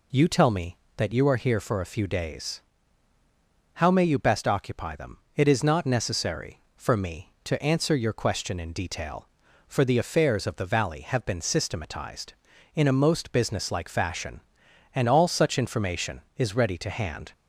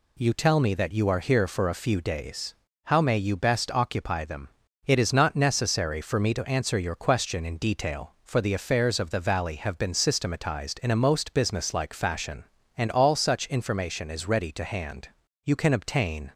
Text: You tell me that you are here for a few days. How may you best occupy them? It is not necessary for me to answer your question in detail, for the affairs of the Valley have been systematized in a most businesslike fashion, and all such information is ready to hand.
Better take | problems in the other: first | goes on to say "You can obtain"; noticeable; from 15.4 s on; 0.88 s long

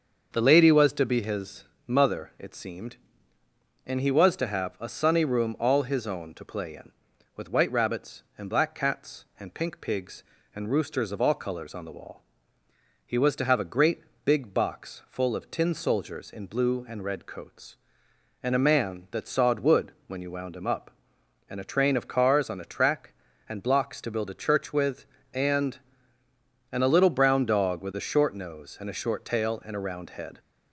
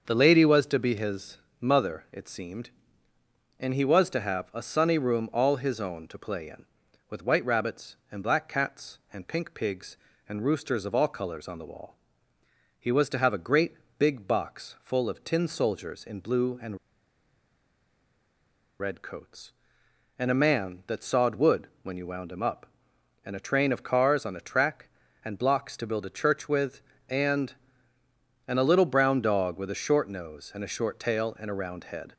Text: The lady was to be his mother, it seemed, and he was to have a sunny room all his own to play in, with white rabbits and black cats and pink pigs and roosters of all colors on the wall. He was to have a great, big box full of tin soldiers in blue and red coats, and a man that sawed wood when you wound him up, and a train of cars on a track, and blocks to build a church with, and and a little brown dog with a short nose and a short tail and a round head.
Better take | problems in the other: first | starts louder than the rest; until 1.0 s; 6.5 dB; also in the first // pauses between "his" and "mother"; slight; at 1.3 s; 0.20 s long; slight in the first // pauses between "and" and "red"; strong; at 16.7 s; 2.0 s long // pauses between "wood" and "when"; slight; at 21.6 s; 0.16 s long; slight in the first

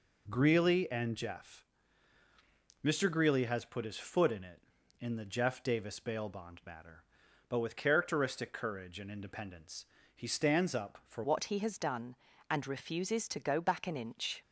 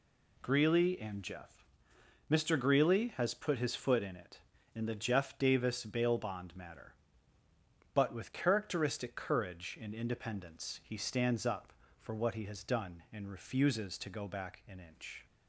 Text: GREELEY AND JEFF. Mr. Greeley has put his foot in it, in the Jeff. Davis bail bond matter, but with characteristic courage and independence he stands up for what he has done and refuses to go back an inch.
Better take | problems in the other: second | pauses between "independence" and "he"; slight; at 9.8 s; 0.32 s long // changes voice at "what"; from 11.2 s on; 3.2 s long

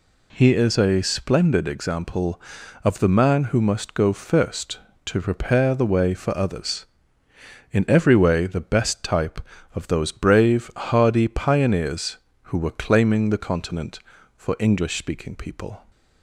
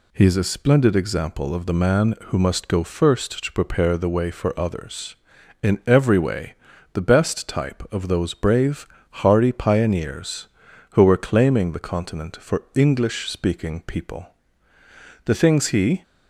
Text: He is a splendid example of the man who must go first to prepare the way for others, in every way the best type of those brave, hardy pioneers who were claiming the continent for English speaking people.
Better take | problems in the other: first | pauses between "way" and "the"; at 6.5 s; 0.40 s long // goes on to say "The things he"; noticeable; from 15.2 s on; 0.76 s long

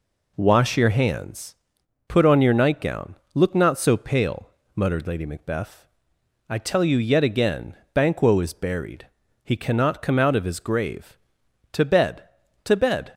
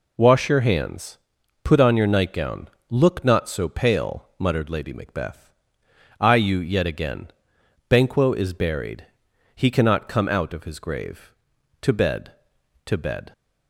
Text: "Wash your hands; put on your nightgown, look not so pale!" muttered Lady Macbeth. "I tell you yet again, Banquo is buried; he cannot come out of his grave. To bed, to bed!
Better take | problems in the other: first | skips "tell"; at 6.3 s

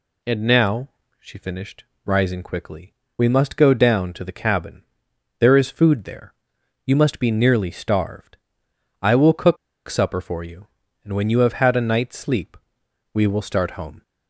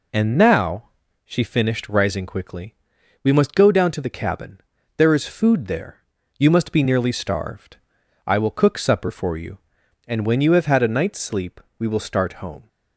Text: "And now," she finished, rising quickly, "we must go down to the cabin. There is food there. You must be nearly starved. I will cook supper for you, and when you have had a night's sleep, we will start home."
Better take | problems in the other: second | pauses between "cook" and "supper"; slight; at 9.5 s; 0.31 s long

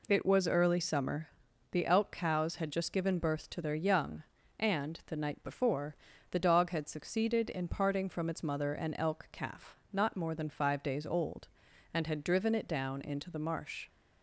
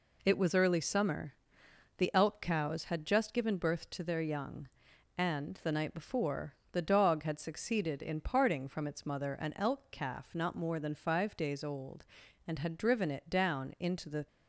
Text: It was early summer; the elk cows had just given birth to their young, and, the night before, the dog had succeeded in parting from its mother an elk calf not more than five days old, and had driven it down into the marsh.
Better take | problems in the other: first | stops before "marsh"; at 14.2 s

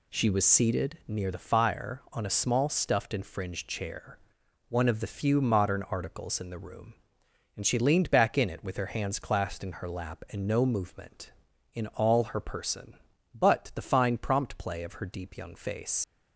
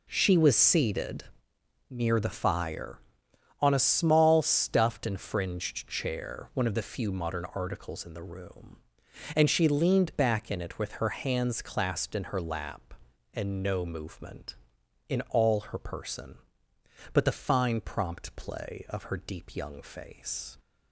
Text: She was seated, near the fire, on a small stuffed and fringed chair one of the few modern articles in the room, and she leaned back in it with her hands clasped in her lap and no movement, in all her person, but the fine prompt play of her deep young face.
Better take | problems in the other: second | pauses between "chair" and "one"; noticeable; at 4.1 s; 0.52 s long // leaves "face" unfinished; at 16.0 s; 125 ms

